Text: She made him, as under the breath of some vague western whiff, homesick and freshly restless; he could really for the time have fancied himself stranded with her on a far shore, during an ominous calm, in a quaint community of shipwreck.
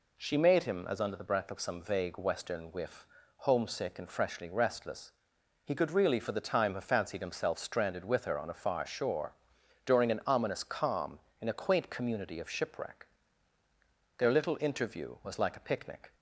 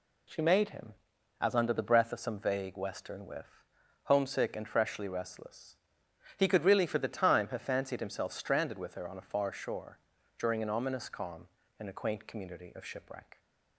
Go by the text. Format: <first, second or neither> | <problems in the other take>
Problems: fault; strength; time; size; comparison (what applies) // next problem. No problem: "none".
second | goes on to say "Their little interview was like a picnic"; strong; from 14.1 s on; 1.9 s long